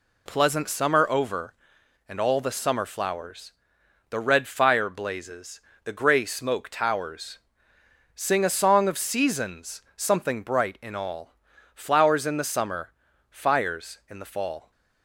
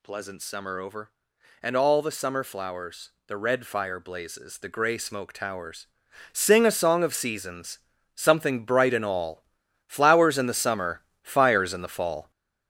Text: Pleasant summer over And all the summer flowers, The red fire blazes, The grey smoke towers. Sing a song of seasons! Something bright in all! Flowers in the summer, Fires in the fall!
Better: first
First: none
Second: gets louder; throughout; 6 dB

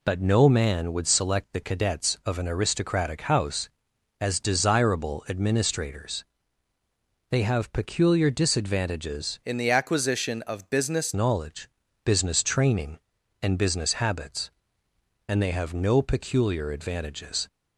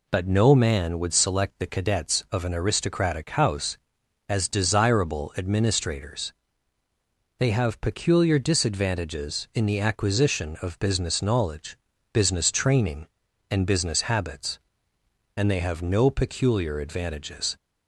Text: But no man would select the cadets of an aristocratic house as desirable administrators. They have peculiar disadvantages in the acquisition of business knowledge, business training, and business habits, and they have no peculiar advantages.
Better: second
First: changes voice from "in" to "business"; from 9.4 to 11.1 s; 1.7 s long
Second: none

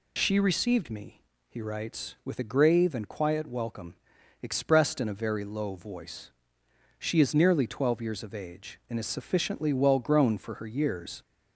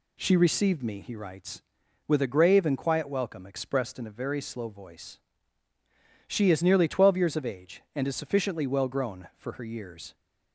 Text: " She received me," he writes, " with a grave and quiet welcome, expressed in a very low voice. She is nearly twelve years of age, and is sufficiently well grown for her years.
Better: first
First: none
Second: says "slow" for "low"; at 4.4 s

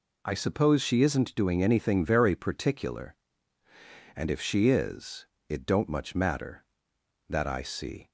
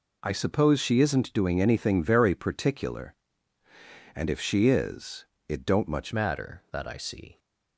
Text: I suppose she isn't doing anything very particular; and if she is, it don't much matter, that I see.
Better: first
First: none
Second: changes voice at "matter"; from 6.1 s on; 1.2 s long

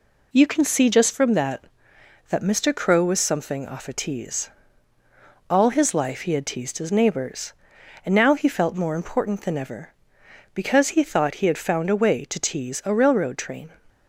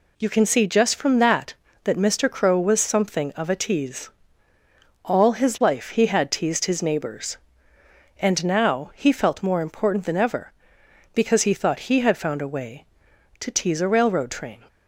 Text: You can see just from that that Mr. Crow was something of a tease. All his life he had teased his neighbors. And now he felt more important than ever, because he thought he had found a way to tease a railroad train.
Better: second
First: says "off" for "of"; at 3.6 s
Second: none

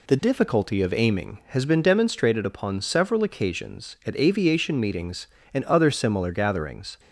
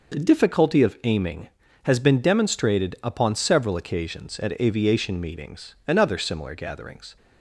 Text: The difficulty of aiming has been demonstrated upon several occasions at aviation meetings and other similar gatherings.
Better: neither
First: none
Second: none

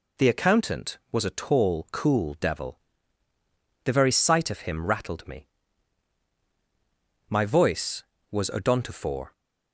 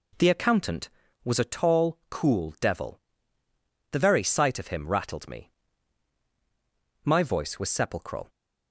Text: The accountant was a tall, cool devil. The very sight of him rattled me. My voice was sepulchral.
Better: second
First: says "odontophore" for "sepulchral"; at 8.5 s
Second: none

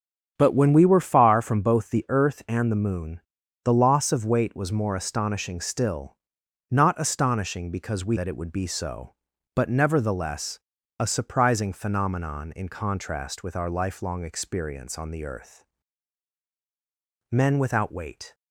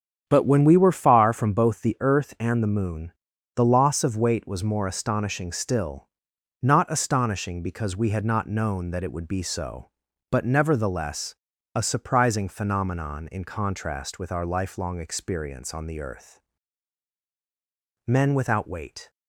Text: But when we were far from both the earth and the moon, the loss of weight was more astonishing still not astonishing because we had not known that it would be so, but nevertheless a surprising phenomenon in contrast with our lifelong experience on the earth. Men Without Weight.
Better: second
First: starts louder than the rest; strong; until 1.3 s; 8 dB // pauses between "still" and "not"; noticeable; at 6.1 s; 0.56 s long // skips "had not known"; at 8.1 s // pauses between "nevertheless" and "a"; at 10.5 s; 0.40 s long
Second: starts louder than the rest; strong; until 1.2 s; 8.5 dB // pauses between "still" and "not"; noticeable; at 6.0 s; 0.56 s long // pauses between "nevertheless" and "a"; at 11.3 s; 0.40 s long

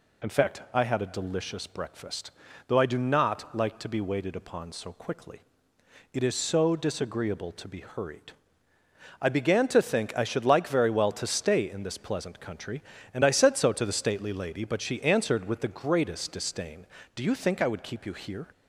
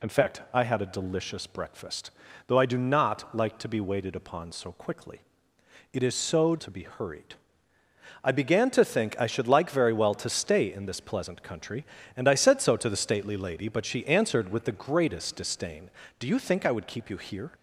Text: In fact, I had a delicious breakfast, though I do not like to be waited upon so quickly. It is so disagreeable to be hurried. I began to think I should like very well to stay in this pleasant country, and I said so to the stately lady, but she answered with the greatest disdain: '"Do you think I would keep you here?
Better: first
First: none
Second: skips "disagreeable"; at 6.5 s

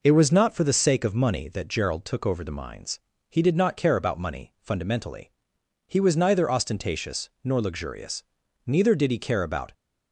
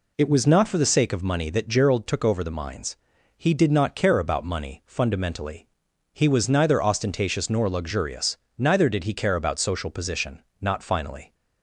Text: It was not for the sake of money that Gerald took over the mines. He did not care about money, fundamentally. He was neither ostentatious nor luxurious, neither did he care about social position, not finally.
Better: second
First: pauses between "ostentatious" and "nor"; slight; at 7.2 s; 0.16 s long // stops before "social position not finally"; at 9.7 s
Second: none

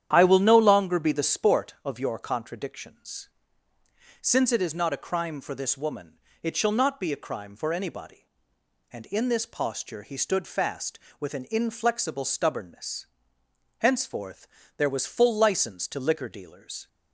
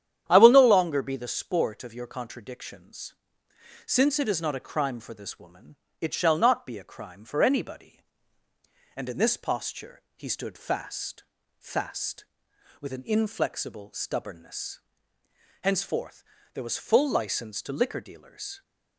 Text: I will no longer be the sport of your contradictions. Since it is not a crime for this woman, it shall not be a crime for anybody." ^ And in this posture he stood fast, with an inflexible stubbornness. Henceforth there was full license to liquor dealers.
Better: first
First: starts louder than the rest; strong; until 1.1 s; 10 dB // pauses between "Henceforth" and "there"; slight; at 14.4 s; 0.28 s long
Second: starts louder than the rest; strong; until 1.2 s; 9.5 dB // pauses between "posture" and "he"; slight; at 9.9 s; 0.16 s long // says "fast" twice; at 11.5 s // pauses between "Henceforth" and "there"; slight; at 16.2 s; 0.30 s long

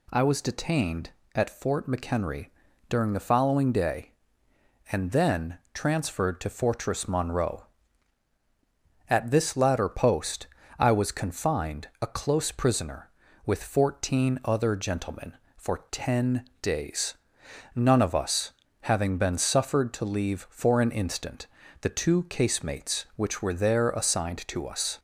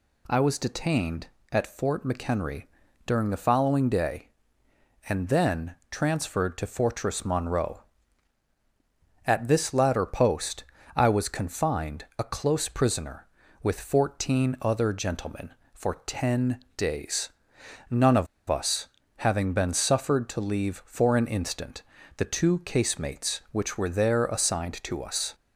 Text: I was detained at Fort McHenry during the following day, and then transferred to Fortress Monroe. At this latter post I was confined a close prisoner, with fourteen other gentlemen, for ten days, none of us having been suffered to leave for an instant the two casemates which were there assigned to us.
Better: first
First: pauses between "McHenry" and "during"; at 2.4 s; 0.42 s long // pauses between "then" and "transferred"; slight; at 5.5 s; 0.16 s long // pauses between "post" and "I"; slight; at 10.4 s; 0.32 s long // pauses between "ten" and "days"; slight; at 16.4 s; 0.18 s long // pauses between "us" and "having"; slight; at 18.5 s; 0.30 s long // pauses between "instant" and "the"; slight; at 21.4 s; 0.34 s long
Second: pauses between "McHenry" and "during"; at 2.6 s; 0.42 s long // pauses between "then" and "transferred"; slight; at 5.7 s; 0.16 s long // pauses between "post" and "I"; slight; at 10.6 s; 0.32 s long // pauses between "ten" and "days"; slight; at 16.5 s; 0.18 s long // pauses between "of" and "us"; slight; at 18.2 s; 0.22 s long // pauses between "us" and "having"; slight; at 18.8 s; 0.30 s long // pauses between "instant" and "the"; slight; at 21.8 s; 0.34 s long

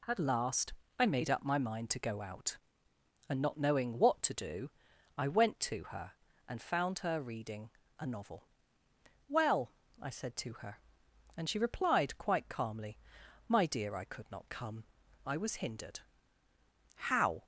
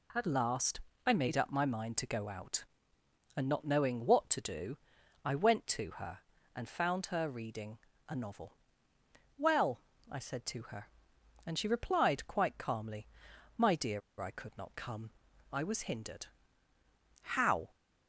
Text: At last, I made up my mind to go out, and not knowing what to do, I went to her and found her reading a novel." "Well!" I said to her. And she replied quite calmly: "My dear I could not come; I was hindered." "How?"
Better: first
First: pauses between "reading" and "a"; slight; at 7.7 s; 0.29 s long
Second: pauses between "reading" and "a"; slight; at 7.7 s; 0.30 s long // pauses between "dear" and "I"; slight; at 14.0 s; 0.19 s long

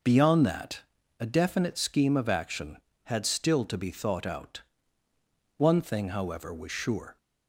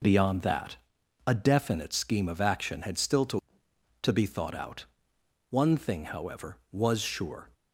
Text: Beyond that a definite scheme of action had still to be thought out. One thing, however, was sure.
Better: first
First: pauses between "that" and "a"; at 0.8 s; 0.38 s long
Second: pauses between "that" and "a"; noticeable; at 0.7 s; 0.50 s long // says "to" twice; at 4.0 s

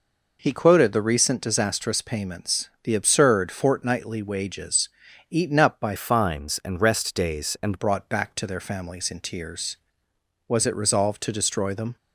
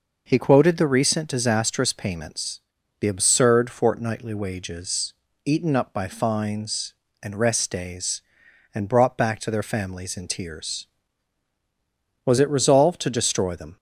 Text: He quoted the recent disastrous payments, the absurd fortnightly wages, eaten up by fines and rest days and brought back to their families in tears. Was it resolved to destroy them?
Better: second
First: changes voice from "fines" to "and"; from 5.9 to 7.8 s; 1.9 s long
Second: none

